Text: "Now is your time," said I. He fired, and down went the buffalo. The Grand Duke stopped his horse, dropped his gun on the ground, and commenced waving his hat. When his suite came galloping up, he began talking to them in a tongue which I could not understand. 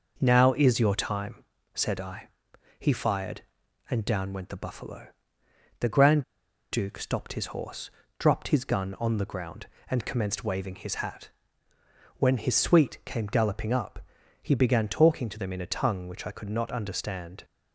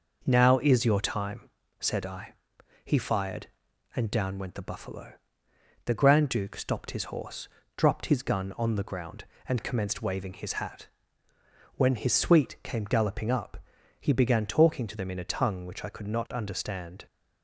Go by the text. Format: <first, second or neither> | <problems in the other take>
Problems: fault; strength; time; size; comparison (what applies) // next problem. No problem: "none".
second | pauses between "Grand" and "Duke"; noticeable; at 6.2 s; 0.48 s long